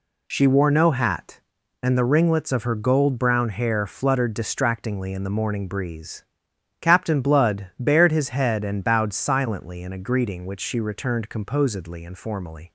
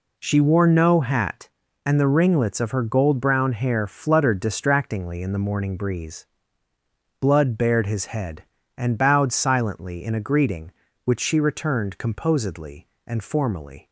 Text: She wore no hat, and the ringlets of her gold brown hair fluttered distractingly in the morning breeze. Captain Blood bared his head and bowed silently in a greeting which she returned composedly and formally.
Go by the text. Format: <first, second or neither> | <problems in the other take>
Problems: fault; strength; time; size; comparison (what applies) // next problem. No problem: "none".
first | skips "Captain"; at 6.7 s